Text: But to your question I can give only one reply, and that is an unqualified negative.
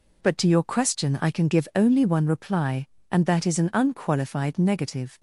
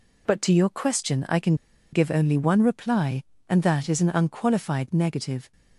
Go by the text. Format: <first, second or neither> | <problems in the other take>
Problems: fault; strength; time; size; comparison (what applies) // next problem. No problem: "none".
first | pauses between "can" and "give"; at 1.5 s; 0.38 s long